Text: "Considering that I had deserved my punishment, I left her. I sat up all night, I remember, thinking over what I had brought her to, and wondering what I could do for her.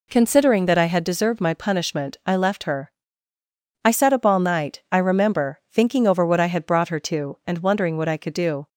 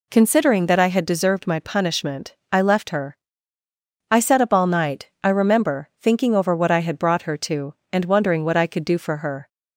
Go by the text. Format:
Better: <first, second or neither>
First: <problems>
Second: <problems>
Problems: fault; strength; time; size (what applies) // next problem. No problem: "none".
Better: second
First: stops before "for her"; at 8.6 s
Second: none